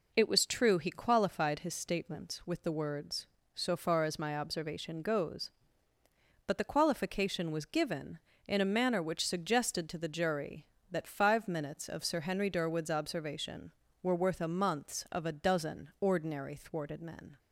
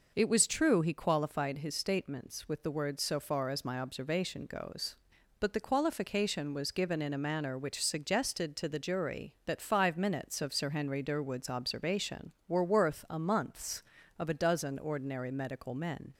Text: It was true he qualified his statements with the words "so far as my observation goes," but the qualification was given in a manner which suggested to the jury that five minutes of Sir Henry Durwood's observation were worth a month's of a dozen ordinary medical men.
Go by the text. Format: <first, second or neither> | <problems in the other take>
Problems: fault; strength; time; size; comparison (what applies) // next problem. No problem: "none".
second | says "thwarted" for "medical"; at 16.5 s